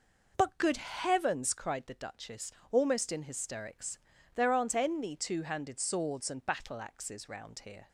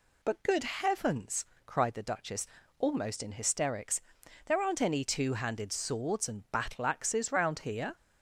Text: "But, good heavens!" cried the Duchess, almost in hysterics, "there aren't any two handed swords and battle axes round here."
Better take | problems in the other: neither | none

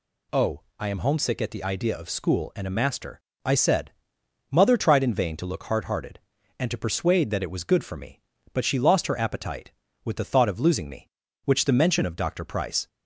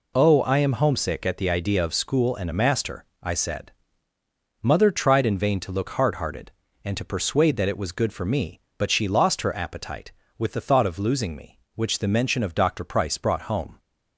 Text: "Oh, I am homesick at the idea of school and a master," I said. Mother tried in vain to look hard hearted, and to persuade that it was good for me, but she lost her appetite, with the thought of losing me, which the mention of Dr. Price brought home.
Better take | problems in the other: second | stops before "brought home"; at 12.8 s

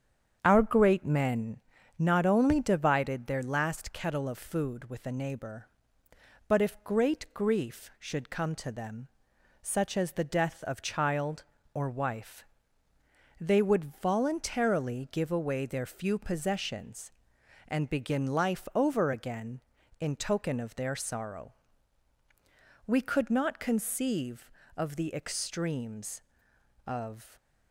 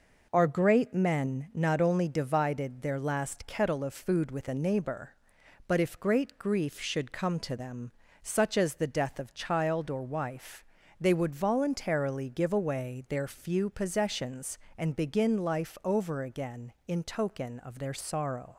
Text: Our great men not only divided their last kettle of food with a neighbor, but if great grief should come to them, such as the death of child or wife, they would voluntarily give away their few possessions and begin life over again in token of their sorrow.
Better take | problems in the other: second | starts louder than the rest; strong; until 1.4 s; 7.5 dB // pauses between "men" and "not"; at 1.5 s; 0.40 s long // goes on to say "We could not conceive of the extremes of"; strong; from 22.8 s on; 4.4 s long

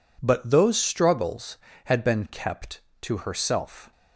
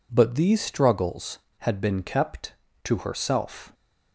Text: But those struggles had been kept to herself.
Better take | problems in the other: first | says "these" for "those"; at 0.3 s

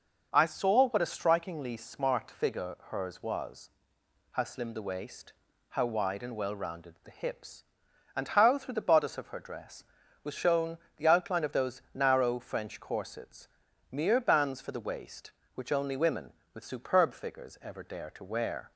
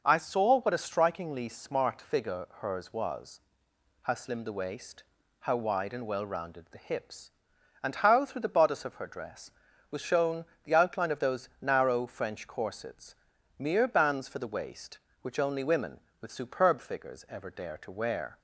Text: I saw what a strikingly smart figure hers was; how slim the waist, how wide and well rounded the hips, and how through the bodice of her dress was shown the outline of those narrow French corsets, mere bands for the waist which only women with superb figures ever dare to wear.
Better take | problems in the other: neither | pauses between "figure" and "hers"; slight; the same in both // pauses between "shown" and "the"; slight; the same in both

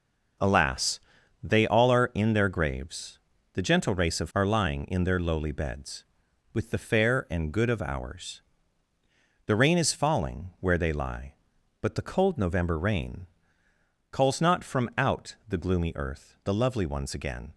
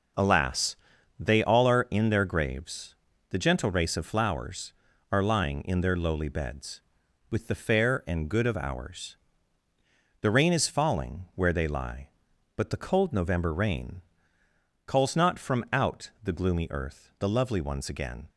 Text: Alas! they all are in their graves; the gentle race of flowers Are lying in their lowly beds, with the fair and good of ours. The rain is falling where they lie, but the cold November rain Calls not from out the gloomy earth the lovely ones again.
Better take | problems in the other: second | skips "flowers"; at 4.3 s // pauses between "rain" and "Calls"; noticeable; at 13.2 s; 0.84 s long; noticeable in the second

